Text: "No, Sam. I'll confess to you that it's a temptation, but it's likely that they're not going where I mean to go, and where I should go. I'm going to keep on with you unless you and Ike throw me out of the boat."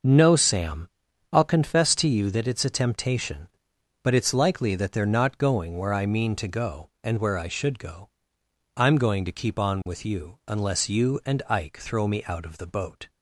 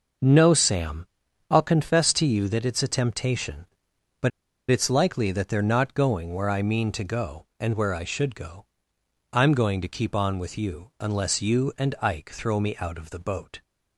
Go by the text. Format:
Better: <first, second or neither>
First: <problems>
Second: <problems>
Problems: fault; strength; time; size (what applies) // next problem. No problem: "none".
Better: first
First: none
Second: pauses between "but" and "it's"; at 4.3 s; 0.39 s long